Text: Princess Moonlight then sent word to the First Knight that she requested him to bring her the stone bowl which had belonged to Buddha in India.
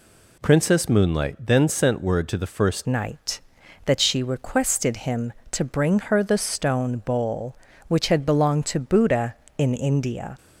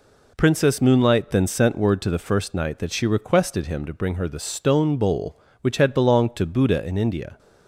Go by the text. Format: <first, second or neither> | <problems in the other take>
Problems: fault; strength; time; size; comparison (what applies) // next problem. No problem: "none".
second | changes voice at "Knight"; from 2.8 s on; 7.5 s long